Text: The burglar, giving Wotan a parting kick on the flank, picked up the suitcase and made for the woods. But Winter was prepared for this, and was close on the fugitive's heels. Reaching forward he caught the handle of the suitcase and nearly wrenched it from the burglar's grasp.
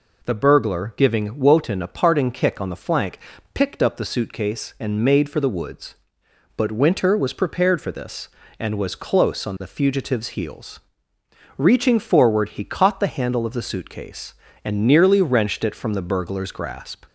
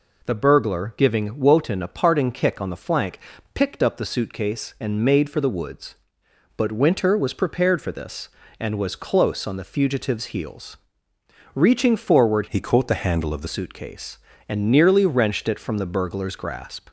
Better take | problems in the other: first | changes voice from "he" to "the"; from 12.4 to 13.4 s; 1.0 s long

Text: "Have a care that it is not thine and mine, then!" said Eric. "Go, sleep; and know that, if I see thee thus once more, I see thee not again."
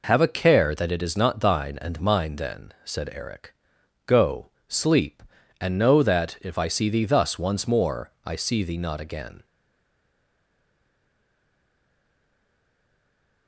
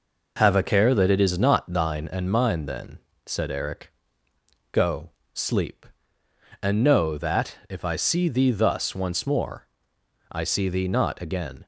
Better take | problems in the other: second | stays silent after the last word; strong; from 9.4 s on; 4.0 s long

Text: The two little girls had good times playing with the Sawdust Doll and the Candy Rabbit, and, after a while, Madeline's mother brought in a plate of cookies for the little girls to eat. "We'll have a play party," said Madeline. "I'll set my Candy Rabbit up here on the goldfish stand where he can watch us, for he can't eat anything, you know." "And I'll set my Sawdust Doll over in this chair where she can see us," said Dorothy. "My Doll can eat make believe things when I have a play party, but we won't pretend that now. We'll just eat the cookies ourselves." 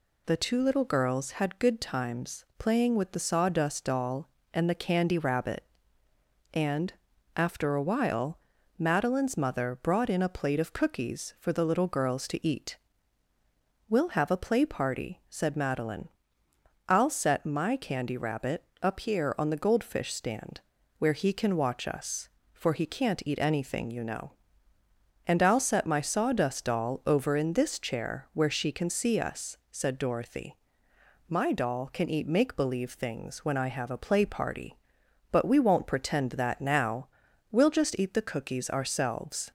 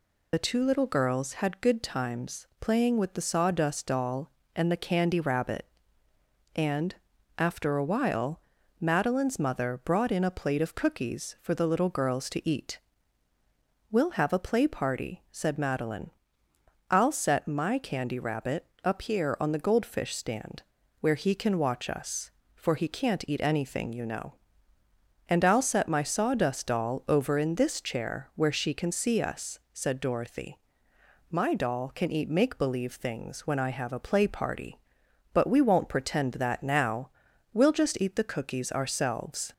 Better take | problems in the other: first | loses the start of "The"; at 0.3 s; 45 ms // pauses between "Rabbit" and "up"; slight; at 18.6 s; 0.20 s long; slight in the first // pauses between "stand" and "where"; at 20.6 s; 0.38 s long; also in the first

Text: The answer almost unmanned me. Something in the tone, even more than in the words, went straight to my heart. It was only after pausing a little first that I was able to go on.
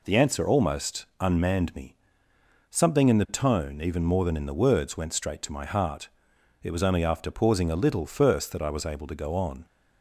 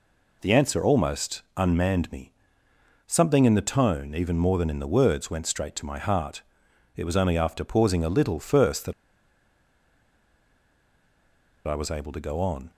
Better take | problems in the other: first | pauses between "that" and "I"; strong; at 8.9 s; 2.7 s long

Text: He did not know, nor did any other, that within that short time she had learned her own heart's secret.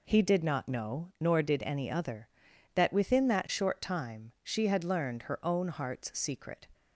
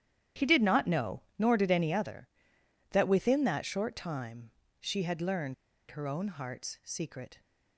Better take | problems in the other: first | starts louder than the rest; strong; until 1.5 s; 11 dB // pauses between "time" and "she"; slight; at 4.5 s; 0.28 s long // pauses between "learned" and "her"; at 5.5 s; 0.36 s long

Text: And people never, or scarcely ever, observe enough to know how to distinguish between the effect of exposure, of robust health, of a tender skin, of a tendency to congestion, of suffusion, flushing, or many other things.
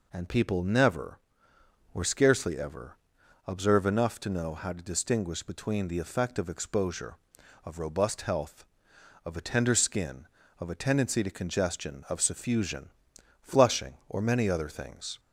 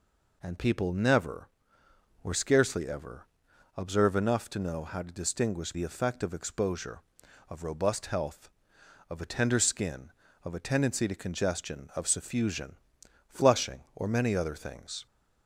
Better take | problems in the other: first | skips "between"; at 5.7 s

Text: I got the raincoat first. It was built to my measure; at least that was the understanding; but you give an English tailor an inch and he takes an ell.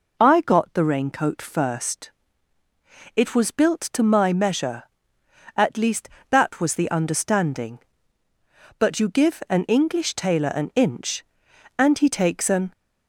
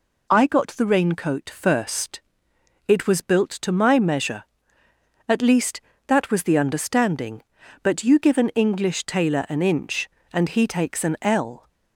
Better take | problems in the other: second | stops before "ell"; at 12.7 s

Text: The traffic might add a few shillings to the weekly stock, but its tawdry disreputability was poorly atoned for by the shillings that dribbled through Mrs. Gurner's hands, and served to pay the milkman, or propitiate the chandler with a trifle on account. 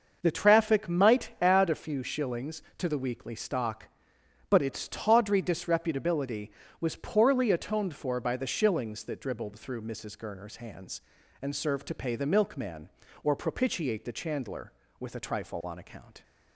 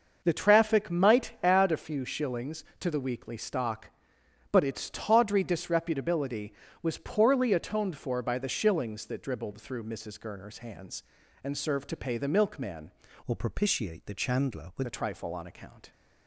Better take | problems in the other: first | starts louder than the rest; noticeable; until 1.2 s; 6 dB; noticeable in the first // changes voice from "or" to "with"; from 13.2 to 14.8 s; 1.6 s long

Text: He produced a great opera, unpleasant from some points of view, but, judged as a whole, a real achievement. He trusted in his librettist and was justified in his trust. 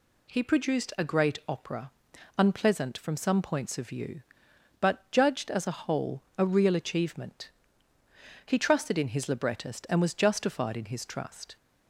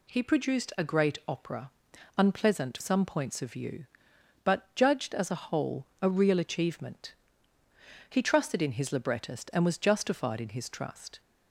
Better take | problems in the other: first | skips "from"; at 2.7 s

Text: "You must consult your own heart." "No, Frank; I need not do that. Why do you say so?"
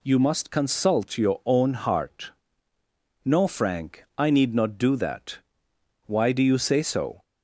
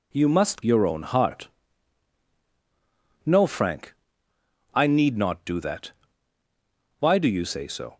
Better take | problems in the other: first | skips "consult"; at 0.6 s

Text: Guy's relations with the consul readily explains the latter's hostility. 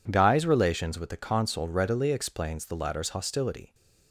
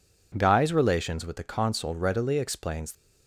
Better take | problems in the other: first | stops before "the latter's hostility"; at 2.9 s

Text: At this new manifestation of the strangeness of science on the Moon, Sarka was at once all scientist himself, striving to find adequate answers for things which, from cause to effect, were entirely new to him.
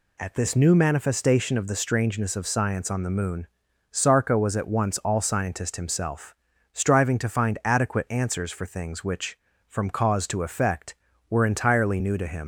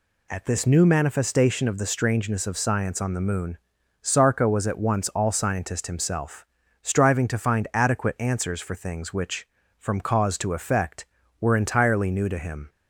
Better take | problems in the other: second | leaves "him" unfinished; at 12.4 s; 100 ms

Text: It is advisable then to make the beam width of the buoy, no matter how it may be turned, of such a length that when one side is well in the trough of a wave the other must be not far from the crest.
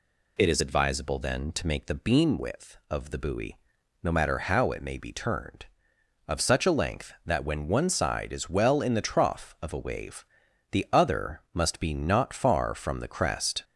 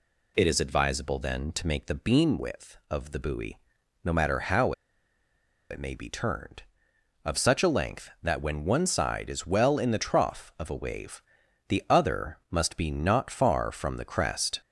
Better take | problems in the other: first | pauses between "how" and "it"; noticeable; at 4.7 s; 0.97 s long // pauses between "wave" and "the"; noticeable; at 11.2 s; 0.46 s long; noticeable in the first

